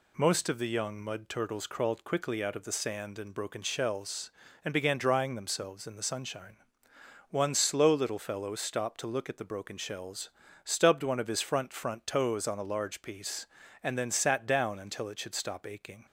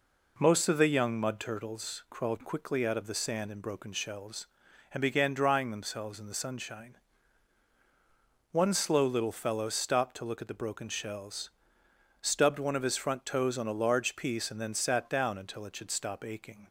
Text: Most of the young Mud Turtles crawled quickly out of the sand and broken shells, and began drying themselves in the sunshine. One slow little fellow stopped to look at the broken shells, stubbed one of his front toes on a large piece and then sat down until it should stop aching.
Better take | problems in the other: second | says "front" twice; at 11.7 s

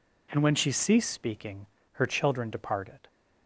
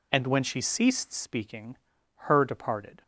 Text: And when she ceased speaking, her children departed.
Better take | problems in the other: first | skips "children"; at 2.4 s

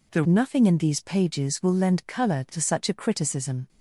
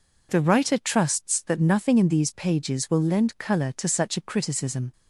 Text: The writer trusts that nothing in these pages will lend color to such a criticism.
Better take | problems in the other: second | skips "writer trusts that"; at 0.2 s

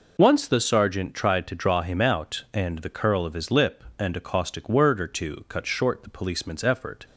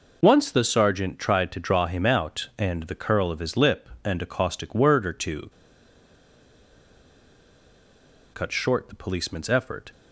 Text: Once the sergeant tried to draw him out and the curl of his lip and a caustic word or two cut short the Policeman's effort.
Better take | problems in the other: first | pauses between "two" and "cut"; strong; at 5.5 s; 2.8 s long

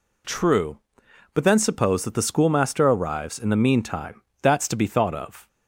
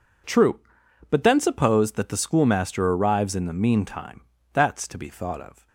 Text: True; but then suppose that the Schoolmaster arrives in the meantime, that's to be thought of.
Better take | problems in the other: neither | none

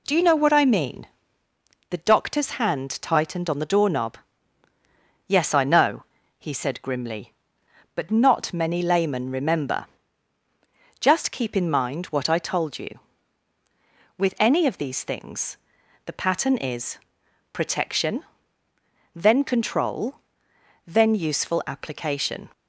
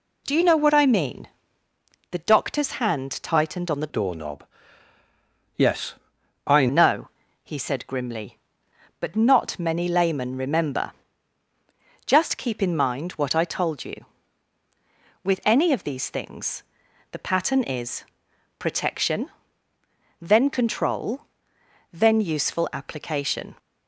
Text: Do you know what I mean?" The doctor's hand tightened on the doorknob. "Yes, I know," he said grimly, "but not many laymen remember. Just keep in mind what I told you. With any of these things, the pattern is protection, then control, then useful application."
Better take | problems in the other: first | changes voice from "doorknob" to "I"; from 3.8 to 6.6 s; 2.8 s long // pauses between "is" and "protection"; noticeable; at 18.0 s; 0.54 s long; noticeable in the first

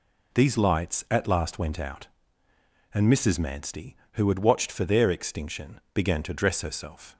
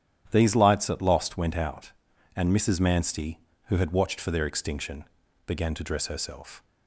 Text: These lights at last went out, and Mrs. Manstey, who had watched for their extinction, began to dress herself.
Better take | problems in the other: first | starts louder than the rest; strong; until 1.3 s; 11 dB // says "lost" for "last"; at 1.0 s

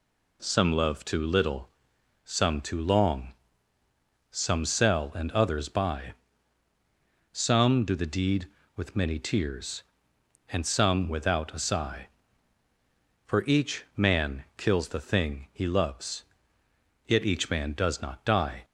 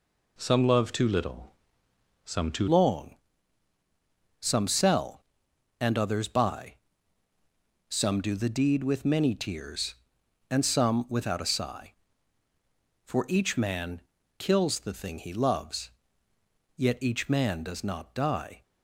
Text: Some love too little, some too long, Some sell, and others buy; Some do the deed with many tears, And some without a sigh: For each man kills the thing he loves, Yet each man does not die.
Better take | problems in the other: first | changes voice at "long"; from 2.6 s on; 16.0 s long // pauses between "man" and "kills"; at 14.0 s; 0.38 s long

